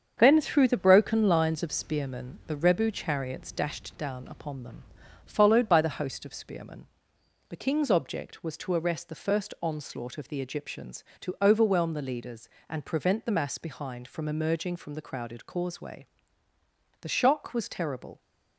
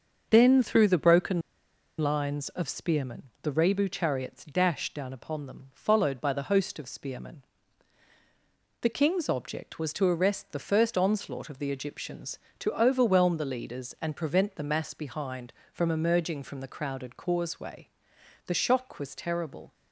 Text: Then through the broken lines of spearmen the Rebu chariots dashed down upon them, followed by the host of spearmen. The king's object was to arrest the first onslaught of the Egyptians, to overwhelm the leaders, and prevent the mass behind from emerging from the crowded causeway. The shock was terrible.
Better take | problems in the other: first | starts louder than the rest; until 1.3 s; 6.5 dB; strong in the first // pauses between "broken" and "lines"; noticeable; at 1.4 s; 0.57 s long // pauses between "spearmen" and "the"; slight; at 3.2 s; 0.18 s long

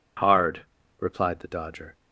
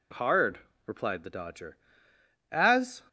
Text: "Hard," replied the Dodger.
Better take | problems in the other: first | goes on to say "As"; from 2.5 s on; 0.50 s long

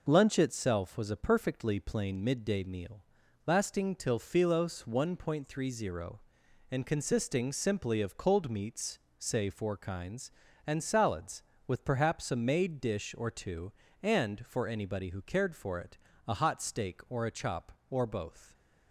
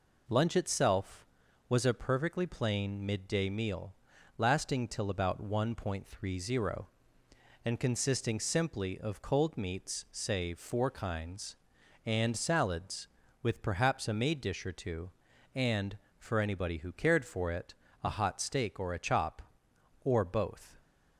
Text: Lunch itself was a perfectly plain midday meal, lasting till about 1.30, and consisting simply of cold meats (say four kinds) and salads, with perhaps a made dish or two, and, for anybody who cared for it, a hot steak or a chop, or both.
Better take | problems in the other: second | says "philos" for "about"; at 4.1 s

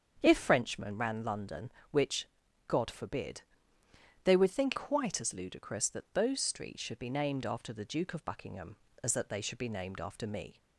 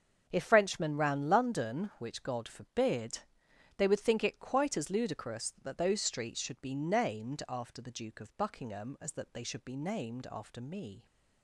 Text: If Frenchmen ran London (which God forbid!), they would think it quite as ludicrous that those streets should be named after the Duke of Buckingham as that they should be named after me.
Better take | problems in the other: second | starts louder than the rest; strong; until 1.2 s; 7.5 dB; also in the second // pauses between "which" and "God"; at 2.2 s; 0.40 s long // skips "it"; at 4.7 s

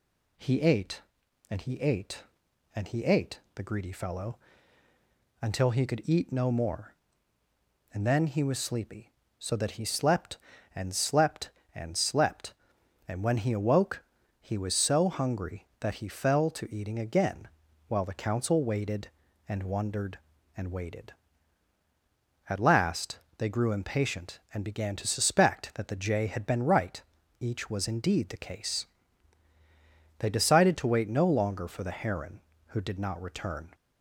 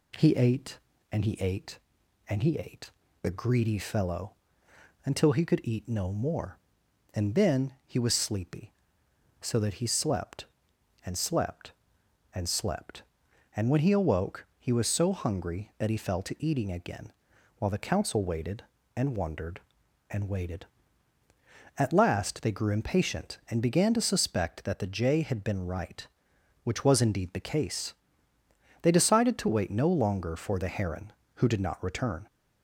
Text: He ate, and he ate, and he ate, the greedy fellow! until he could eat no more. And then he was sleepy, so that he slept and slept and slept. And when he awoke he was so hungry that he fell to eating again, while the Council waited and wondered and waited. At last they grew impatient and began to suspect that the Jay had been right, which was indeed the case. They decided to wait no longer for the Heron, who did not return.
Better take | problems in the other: second | pauses between "awoke" and "he"; at 14.0 s; 0.38 s long // pauses between "last" and "they"; slight; at 23.1 s; 0.18 s long // says "each" for "which"; at 27.3 s

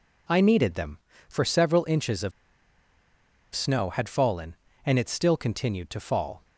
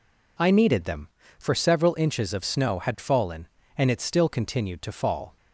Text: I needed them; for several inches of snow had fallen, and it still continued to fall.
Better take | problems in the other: second | pauses between "of" and "snow"; at 2.3 s; 1.2 s long

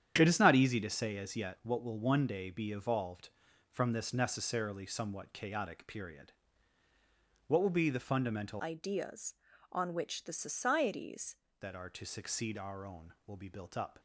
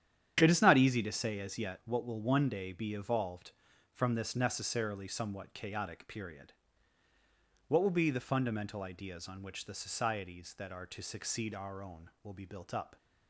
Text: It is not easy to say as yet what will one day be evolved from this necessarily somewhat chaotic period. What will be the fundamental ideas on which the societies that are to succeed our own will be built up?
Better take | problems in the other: second | starts louder than the rest; strong; until 1.1 s; 9 dB; strong in the second // changes voice from "ideas" to "societies"; from 8.6 to 11.3 s; 2.7 s long

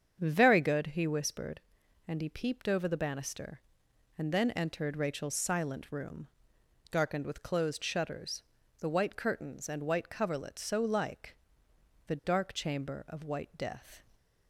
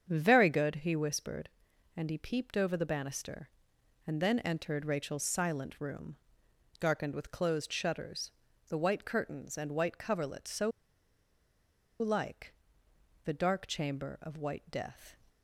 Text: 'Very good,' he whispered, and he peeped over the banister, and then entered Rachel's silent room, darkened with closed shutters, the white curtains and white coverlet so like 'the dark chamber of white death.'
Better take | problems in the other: first | starts louder than the rest; strong; until 1.1 s; 7.5 dB; strong in the first // pauses between "so" and "like"; strong; at 10.7 s; 1.2 s long // pauses between "like" and "the"; noticeable; at 12.5 s; 0.70 s long; noticeable in the first

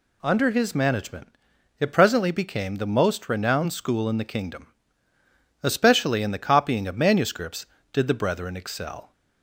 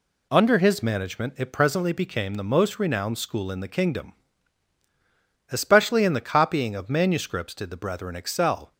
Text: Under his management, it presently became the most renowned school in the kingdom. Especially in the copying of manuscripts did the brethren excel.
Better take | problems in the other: neither | none

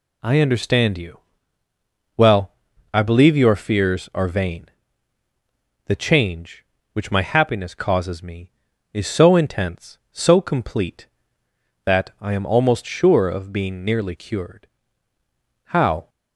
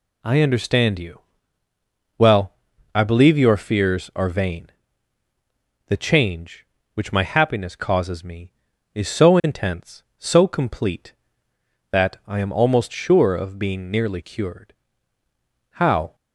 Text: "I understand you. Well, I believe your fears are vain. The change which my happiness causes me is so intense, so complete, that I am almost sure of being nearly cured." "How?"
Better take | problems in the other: neither | none

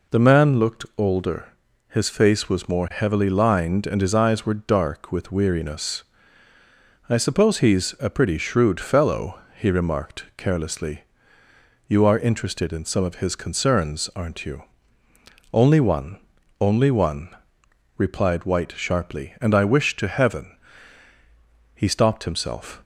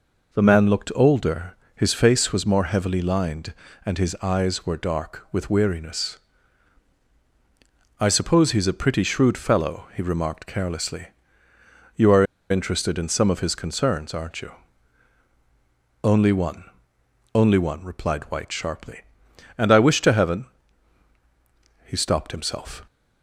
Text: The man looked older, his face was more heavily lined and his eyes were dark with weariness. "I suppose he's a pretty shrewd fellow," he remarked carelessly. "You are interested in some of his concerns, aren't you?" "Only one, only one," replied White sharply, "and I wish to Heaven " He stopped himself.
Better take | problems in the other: first | pauses between "are" and "interested"; slight; at 12.2 s; 0.26 s long

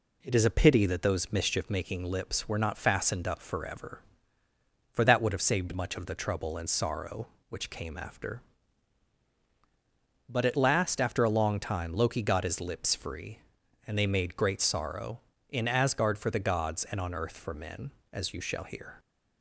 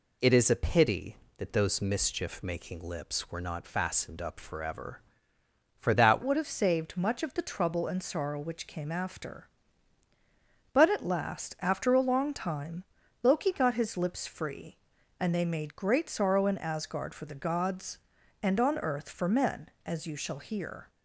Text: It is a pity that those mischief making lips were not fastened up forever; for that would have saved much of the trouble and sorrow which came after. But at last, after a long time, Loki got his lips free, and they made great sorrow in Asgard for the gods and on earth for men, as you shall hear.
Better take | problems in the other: first | changes voice at "would"; from 6.2 s on; 14.6 s long

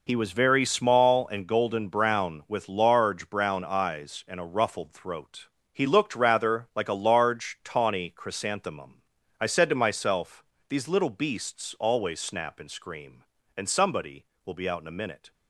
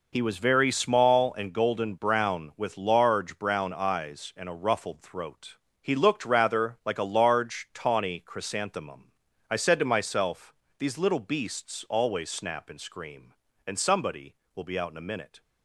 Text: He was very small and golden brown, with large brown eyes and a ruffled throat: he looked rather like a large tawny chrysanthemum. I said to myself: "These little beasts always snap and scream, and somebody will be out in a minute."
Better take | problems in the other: neither | none

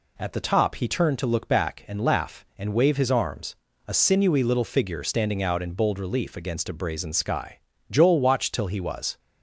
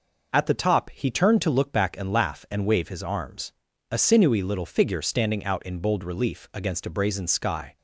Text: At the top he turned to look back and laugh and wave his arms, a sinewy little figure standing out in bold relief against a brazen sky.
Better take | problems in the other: second | goes on to say "Joel watched till he was"; noticeable; from 7.8 s on; 1.2 s long

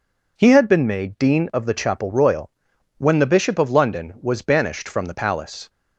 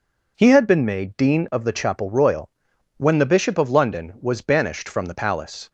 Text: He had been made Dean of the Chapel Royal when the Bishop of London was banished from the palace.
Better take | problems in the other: neither | pauses between "Royal" and "when"; noticeable; the same in both

